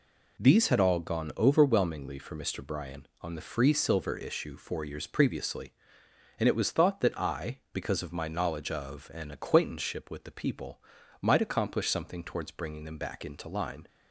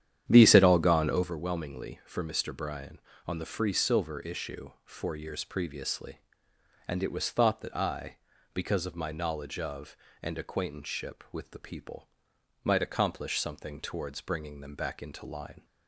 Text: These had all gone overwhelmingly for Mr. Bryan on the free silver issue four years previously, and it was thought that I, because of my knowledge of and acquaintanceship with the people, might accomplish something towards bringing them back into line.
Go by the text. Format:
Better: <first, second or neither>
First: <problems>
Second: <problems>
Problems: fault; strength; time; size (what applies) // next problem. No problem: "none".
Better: first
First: none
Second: starts louder than the rest; strong; until 1.4 s; 9.5 dB